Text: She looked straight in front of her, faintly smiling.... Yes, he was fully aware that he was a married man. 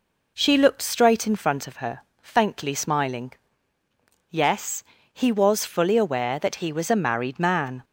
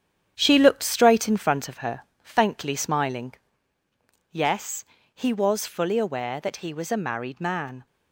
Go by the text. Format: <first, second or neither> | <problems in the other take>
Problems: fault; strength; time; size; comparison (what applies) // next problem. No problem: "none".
first | gets quieter; strong; throughout; 7.5 dB